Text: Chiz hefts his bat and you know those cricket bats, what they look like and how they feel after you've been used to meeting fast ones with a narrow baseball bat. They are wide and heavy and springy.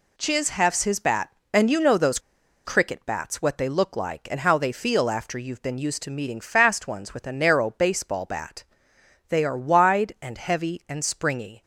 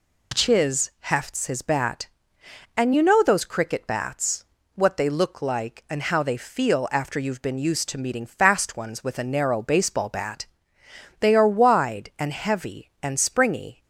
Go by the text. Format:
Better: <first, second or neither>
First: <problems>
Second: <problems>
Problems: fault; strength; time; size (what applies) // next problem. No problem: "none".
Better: second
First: pauses between "those" and "cricket"; noticeable; at 2.1 s; 0.47 s long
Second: none